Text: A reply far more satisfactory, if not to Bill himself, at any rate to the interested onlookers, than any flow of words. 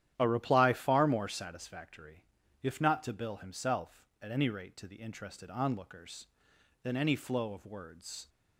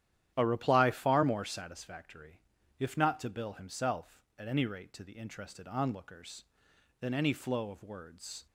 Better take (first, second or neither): neither